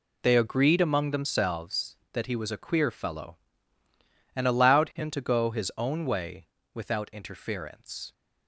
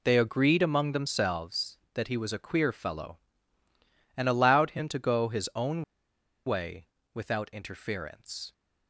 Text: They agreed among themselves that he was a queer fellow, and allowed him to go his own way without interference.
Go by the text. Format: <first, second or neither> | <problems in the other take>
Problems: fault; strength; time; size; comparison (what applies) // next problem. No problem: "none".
first | pauses between "own" and "way"; noticeable; at 5.8 s; 0.62 s long // pauses between "way" and "without"; slight; at 6.8 s; 0.26 s long; slight in the first